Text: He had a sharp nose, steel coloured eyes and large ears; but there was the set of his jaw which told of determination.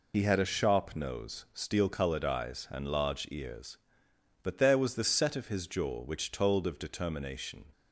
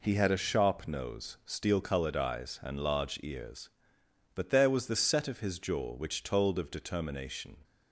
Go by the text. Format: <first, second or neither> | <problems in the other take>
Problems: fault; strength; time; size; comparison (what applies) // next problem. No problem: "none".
second | loses the start of "He"; at 0.1 s; 50 ms